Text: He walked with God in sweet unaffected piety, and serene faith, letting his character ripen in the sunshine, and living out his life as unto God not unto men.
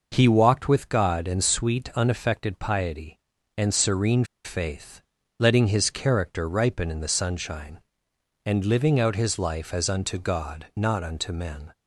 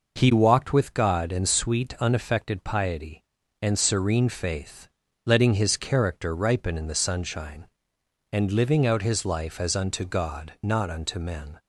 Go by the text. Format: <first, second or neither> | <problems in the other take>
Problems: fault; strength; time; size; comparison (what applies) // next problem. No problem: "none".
second | pauses between "serene" and "faith"; slight; at 4.2 s; 0.19 s long